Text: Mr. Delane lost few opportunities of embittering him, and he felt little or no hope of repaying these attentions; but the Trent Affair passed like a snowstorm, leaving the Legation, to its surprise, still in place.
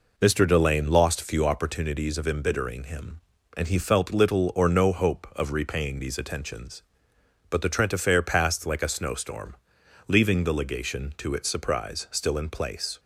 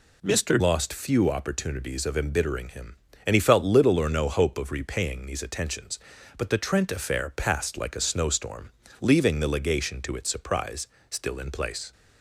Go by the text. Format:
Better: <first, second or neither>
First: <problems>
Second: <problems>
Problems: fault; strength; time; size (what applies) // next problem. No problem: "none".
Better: first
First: none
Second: skips "Delane"; at 0.5 s